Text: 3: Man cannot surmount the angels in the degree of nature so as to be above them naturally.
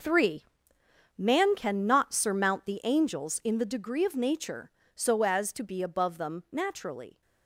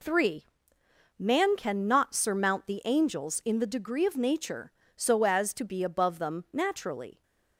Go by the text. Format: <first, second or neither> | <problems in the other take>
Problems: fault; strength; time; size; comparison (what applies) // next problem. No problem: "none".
second | gets quieter; strong; throughout; 11.5 dB